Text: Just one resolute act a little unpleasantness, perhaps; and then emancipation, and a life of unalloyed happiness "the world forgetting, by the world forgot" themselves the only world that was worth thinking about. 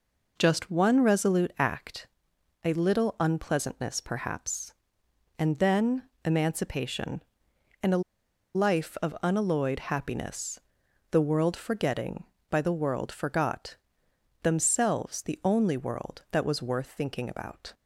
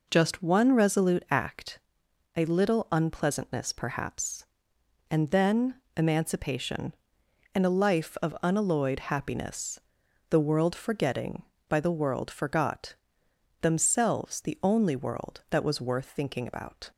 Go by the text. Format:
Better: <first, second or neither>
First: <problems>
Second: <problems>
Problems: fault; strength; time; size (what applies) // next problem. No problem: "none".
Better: second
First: pauses between "act" and "a"; noticeable; at 2.0 s; 0.54 s long // pauses between "then" and "emancipation"; slight; at 6.0 s; 0.24 s long // pauses between "a" and "life"; noticeable; at 8.0 s; 0.54 s long // pauses between "happiness" and "the"; noticeable; at 10.6 s; 0.50 s long // pauses between "forgot" and "themselves"; noticeable; at 13.7 s; 0.68 s long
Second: pauses between "act" and "a"; noticeable; at 1.7 s; 0.54 s long // pauses between "then" and "emancipation"; slight; at 5.7 s; 0.24 s long // pauses between "happiness" and "the"; noticeable; at 9.8 s; 0.48 s long // pauses between "forgot" and "themselves"; noticeable; at 12.9 s; 0.68 s long